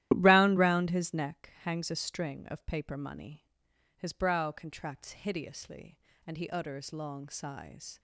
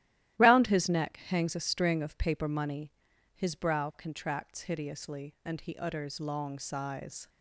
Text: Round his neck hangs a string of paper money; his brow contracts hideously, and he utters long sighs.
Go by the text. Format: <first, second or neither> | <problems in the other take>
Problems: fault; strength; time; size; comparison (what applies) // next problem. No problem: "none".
second | starts louder than the rest; strong; until 1.1 s; 13.5 dB; strong in the second // says "Round" twice; at 0.5 s